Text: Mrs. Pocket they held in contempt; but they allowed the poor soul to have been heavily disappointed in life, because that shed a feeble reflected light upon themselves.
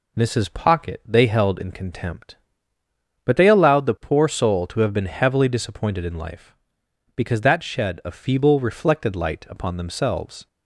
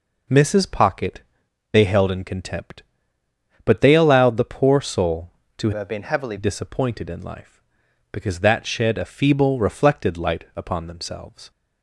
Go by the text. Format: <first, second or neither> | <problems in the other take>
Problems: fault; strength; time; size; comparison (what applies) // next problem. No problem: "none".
first | pauses between "Pocket" and "they"; noticeable; at 1.2 s; 0.50 s long // changes voice from "have" to "heavily"; from 5.7 to 6.3 s; 0.6 s long